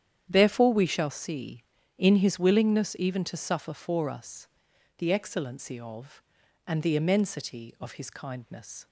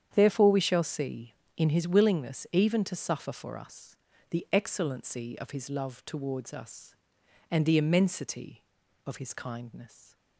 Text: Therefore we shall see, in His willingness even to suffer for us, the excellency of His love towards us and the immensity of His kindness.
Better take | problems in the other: second | starts louder than the rest; strong; until 1.3 s; 9.5 dB; strong in the second // skips "His love towards us"; at 6.4 s

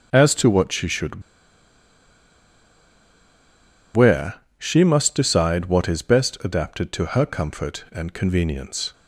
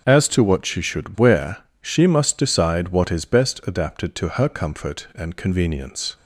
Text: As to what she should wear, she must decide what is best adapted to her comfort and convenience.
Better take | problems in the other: second | starts louder than the rest; noticeable; until 1.1 s; 6 dB; noticeable in the second // pauses between "should" and "wear"; strong; at 1.2 s; 2.7 s long

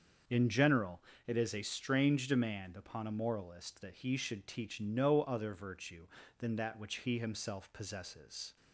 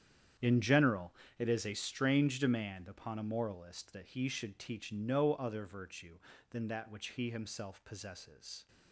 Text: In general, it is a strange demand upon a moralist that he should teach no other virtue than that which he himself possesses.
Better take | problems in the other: first | gets quieter; strong; throughout; 14.5 dB // starts louder than the rest; strong; until 1.6 s; 9 dB; also in the first

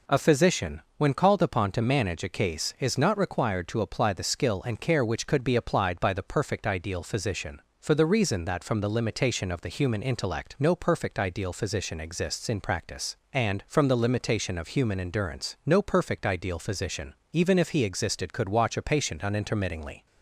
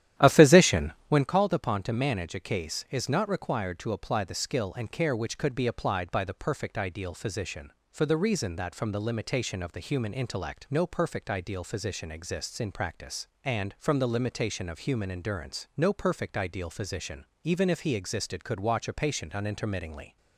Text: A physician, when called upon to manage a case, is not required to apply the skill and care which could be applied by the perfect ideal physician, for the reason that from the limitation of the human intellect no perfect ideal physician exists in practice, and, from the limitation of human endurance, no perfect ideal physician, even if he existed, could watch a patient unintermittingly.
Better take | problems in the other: first | starts louder than the rest; strong; until 1.3 s; 11.5 dB

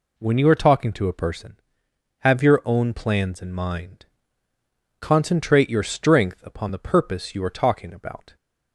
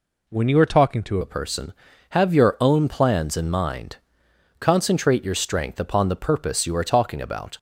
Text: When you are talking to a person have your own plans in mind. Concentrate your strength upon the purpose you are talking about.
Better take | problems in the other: first | changes voice at "a"; from 1.2 s on; 6.3 s long

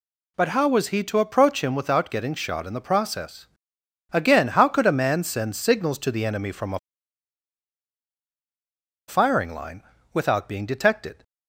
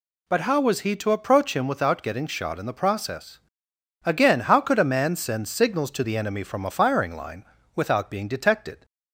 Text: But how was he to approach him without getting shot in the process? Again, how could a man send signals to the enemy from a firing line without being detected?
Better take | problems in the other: second | pauses between "a" and "firing"; strong; at 6.7 s; 2.2 s long // pauses between "line" and "without"; slight; at 9.8 s; 0.30 s long; slight in the second

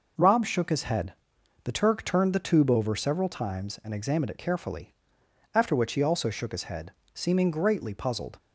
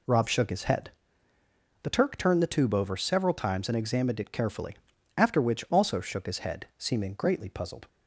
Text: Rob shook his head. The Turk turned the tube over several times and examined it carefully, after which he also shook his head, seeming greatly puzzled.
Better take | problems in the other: first | skips "he"; at 5.6 s

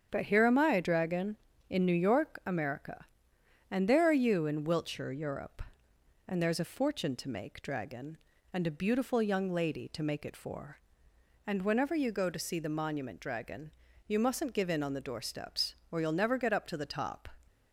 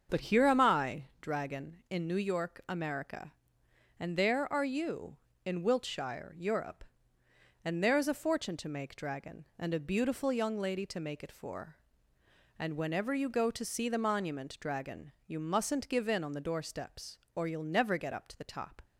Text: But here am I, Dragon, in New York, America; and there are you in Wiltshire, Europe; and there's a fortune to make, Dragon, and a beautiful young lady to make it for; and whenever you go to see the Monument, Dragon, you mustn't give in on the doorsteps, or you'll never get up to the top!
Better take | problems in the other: neither | starts louder than the rest; the same in both

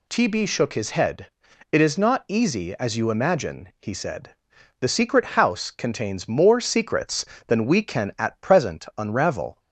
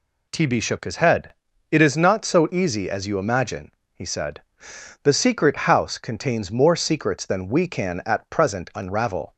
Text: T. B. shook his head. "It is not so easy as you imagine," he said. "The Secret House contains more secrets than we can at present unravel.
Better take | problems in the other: second | skips "so"; at 2.2 s

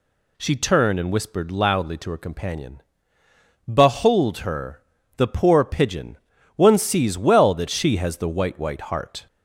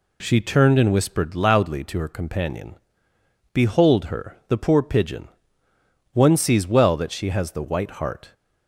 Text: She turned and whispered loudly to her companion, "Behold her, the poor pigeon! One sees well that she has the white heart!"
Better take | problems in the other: second | says "white" twice; at 8.5 s

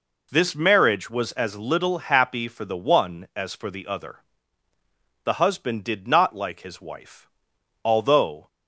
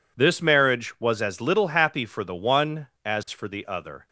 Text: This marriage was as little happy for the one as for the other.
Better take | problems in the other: second | goes on to say "The husband did not like his wife although"; strong; from 5.2 s on; 3.2 s long

